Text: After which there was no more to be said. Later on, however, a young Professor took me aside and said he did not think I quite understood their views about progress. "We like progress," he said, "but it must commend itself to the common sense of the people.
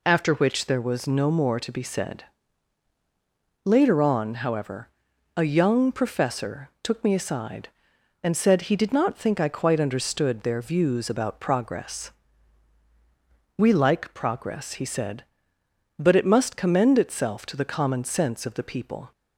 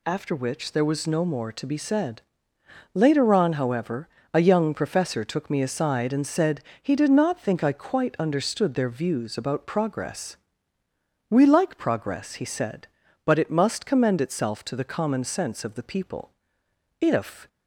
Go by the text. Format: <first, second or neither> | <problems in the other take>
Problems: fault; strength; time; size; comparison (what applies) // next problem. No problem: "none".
first | pauses between "said" and "he"; slight; at 6.6 s; 0.20 s long // goes on to say "If"; slight; from 16.9 s on; 0.48 s long